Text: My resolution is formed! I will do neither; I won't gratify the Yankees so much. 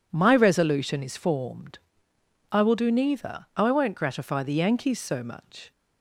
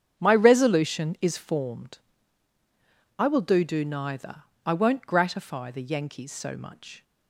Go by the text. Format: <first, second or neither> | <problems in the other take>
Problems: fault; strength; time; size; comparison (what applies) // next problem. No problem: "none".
first | starts louder than the rest; strong; until 1.2 s; 8 dB // says "do" twice; at 3.6 s